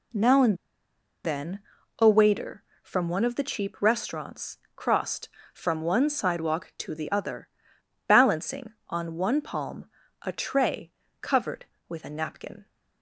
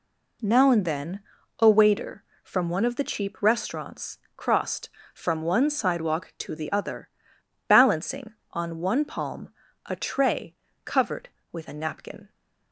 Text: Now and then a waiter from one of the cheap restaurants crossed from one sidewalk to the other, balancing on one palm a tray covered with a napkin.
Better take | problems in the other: second | pauses between "and" and "then"; noticeable; at 0.5 s; 0.68 s long // pauses between "then" and "a"; at 1.5 s; 0.40 s long; also in the second // pauses between "restaurants" and "crossed"; slight; at 4.5 s; 0.16 s long; slight in the second // pauses between "palm" and "a"; slight; at 9.8 s; 0.36 s long; slight in the second // pauses between "tray" and "covered"; slight; at 10.9 s; 0.32 s long; slight in the second

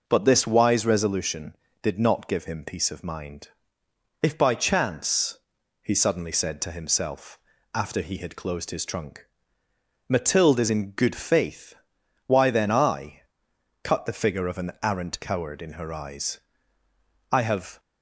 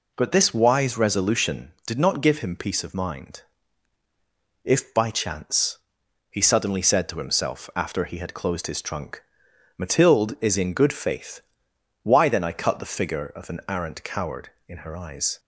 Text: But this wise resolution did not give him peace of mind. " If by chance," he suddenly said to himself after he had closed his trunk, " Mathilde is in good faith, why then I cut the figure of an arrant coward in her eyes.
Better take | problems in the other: second | starts louder than the rest; until 1.0 s; 7 dB // pauses between "himself" and "after"; slight; at 7.3 s; 0.34 s long // pauses between "I" and "cut"; noticeable; at 13.2 s; 0.60 s long // goes on to say "I have"; slight; from 17.3 s on; 0.48 s long

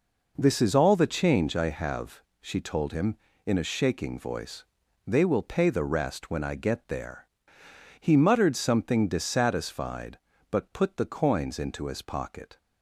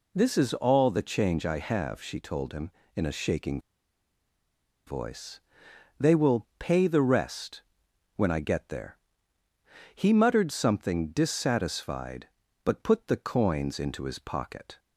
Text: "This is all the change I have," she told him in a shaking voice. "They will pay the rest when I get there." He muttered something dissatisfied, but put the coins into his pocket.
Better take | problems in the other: first | pauses between "shaking" and "voice"; strong; at 3.5 s; 1.2 s long // pauses between "rest" and "when"; noticeable; at 7.6 s; 0.54 s long

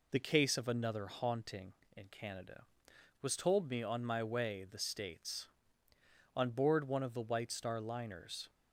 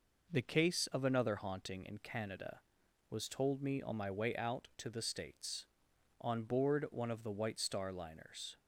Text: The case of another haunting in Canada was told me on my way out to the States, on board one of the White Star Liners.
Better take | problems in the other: second | skips "out to"; at 4.6 s

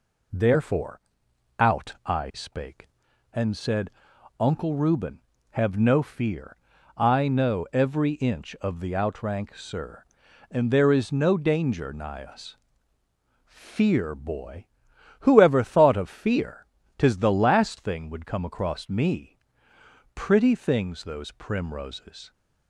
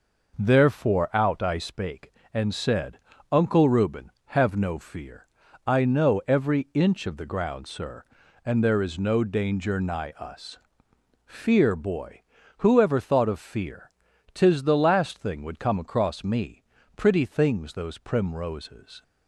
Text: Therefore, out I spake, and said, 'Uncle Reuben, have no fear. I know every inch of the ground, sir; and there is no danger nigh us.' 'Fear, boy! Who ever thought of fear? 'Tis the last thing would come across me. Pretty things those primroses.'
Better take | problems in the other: second | says "outrank" for "ground"; at 8.9 s

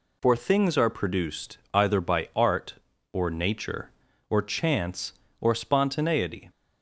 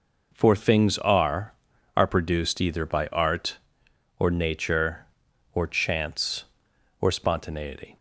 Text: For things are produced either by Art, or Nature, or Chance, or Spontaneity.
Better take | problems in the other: first | says "are" twice; at 1.9 s

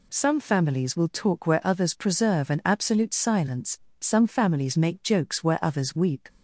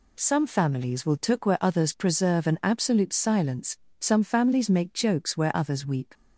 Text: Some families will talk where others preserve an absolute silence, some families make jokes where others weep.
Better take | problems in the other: first | says "took" for "talk"; at 1.1 s

